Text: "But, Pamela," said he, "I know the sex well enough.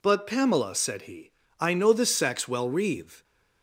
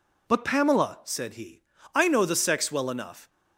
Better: second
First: says "reeve" for "enough"; at 2.6 s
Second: none

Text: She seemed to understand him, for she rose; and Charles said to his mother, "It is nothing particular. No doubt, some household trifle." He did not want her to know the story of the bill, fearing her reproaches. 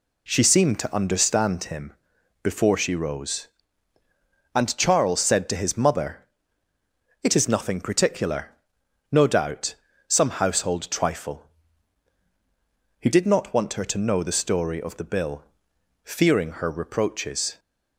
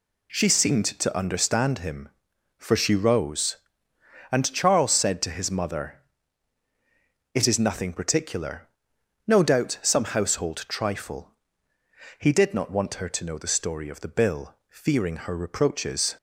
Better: second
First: says "before" for "for"; at 2.4 s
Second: none

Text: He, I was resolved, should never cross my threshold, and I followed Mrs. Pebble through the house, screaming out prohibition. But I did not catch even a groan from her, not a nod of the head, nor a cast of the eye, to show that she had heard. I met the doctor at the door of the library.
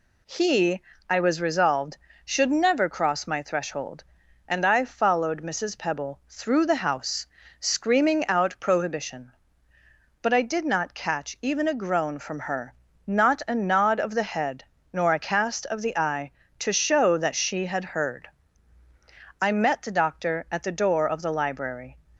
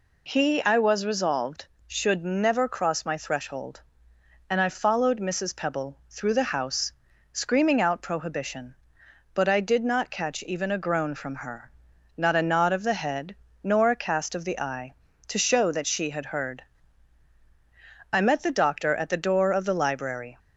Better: neither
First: none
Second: none

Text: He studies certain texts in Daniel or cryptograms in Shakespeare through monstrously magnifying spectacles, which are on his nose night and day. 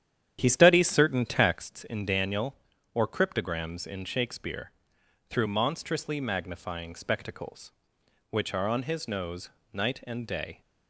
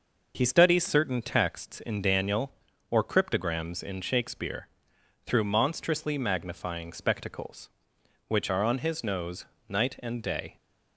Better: second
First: starts louder than the rest; strong; until 1.7 s; 10 dB // pauses between "Shakespeare" and "through"; noticeable; at 4.7 s; 0.56 s long // pauses between "nose" and "night"; slight; at 9.4 s; 0.24 s long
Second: pauses between "Shakespeare" and "through"; noticeable; at 4.6 s; 0.56 s long // pauses between "nose" and "night"; slight; at 9.4 s; 0.24 s long

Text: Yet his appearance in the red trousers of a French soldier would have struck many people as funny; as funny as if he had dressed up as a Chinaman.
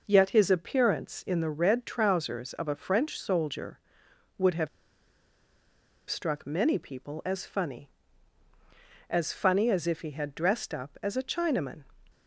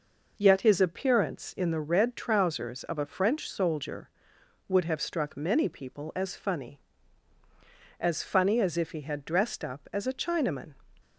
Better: second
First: pauses between "have" and "struck"; strong; at 4.6 s; 1.4 s long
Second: none

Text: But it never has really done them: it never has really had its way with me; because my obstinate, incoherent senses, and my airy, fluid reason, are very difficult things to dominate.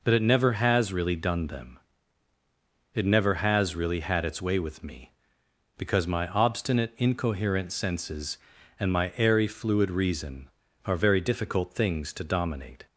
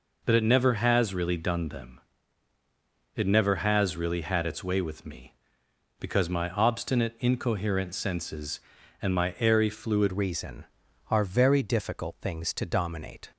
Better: first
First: none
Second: changes voice at "reason"; from 10.1 s on; 3.2 s long

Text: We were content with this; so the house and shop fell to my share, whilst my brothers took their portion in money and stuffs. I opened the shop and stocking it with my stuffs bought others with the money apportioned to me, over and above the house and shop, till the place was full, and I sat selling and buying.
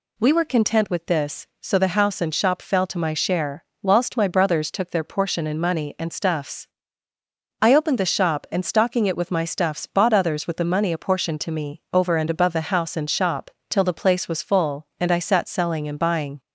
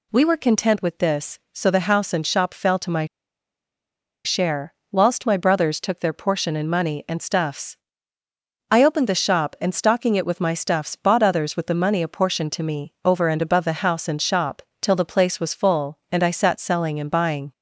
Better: first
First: none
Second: pauses between "my" and "share"; at 3.0 s; 1.2 s long

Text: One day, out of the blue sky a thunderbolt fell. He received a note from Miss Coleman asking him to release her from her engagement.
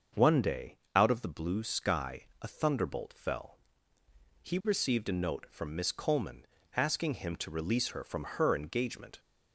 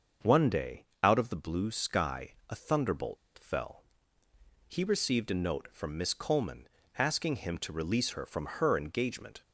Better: first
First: starts louder than the rest; until 1.3 s; 6.5 dB // pauses between "Coleman" and "asking"; slight; at 6.4 s; 0.32 s long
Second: starts louder than the rest; until 1.4 s; 6.5 dB // pauses between "thunderbolt" and "fell"; slight; at 3.1 s; 0.20 s long // pauses between "Coleman" and "asking"; slight; at 6.6 s; 0.32 s long

